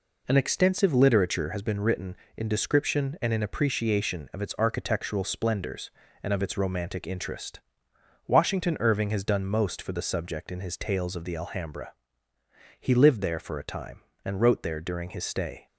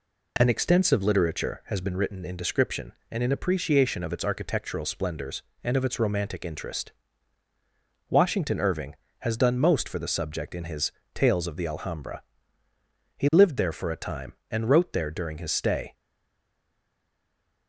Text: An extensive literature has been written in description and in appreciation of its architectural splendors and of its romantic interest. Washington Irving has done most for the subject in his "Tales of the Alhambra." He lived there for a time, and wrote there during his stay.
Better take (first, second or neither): first